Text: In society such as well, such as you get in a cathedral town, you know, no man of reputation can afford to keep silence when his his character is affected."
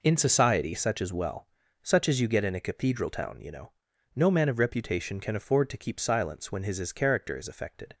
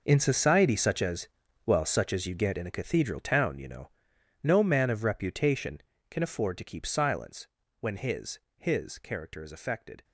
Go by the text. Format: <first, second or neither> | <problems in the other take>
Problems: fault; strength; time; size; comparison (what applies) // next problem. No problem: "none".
first | gets quieter; strong; throughout; 15.5 dB // pauses between "as" and "well"; at 1.2 s; 0.38 s long // pauses between "silence" and "when"; slight; at 7.4 s; 0.32 s long // pauses between "his" and "his"; slight; at 8.3 s; 0.18 s long